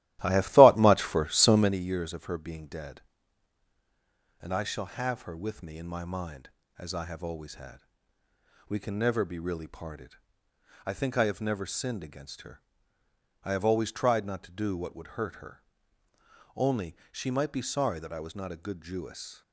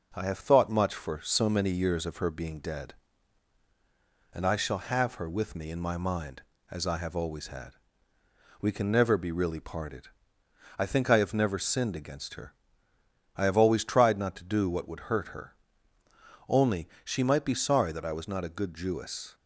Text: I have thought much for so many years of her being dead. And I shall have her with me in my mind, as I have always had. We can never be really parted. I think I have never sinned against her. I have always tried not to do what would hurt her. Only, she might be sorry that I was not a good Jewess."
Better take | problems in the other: second | starts louder than the rest; strong; until 1.8 s; 15 dB

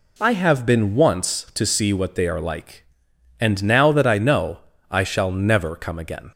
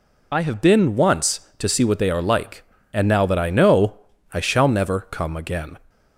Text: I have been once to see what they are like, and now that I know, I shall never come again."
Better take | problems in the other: first | loses the start of "I"; at 0.3 s; 50 ms

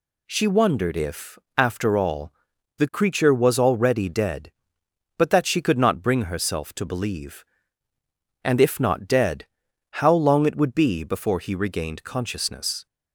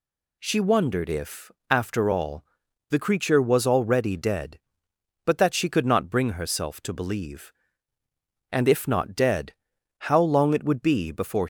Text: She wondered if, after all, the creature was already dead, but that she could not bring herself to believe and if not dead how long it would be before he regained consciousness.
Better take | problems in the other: first | pauses between "dead" and "how"; noticeable; at 9.5 s; 0.56 s long; noticeable in the first // stops before "he regained consciousness"; at 11.4 s

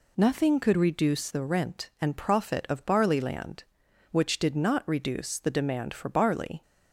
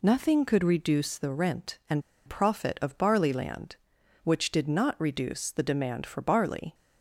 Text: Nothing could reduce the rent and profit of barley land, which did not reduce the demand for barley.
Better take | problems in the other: first | pauses between "and" and "profit"; slight; at 2.0 s; 0.26 s long

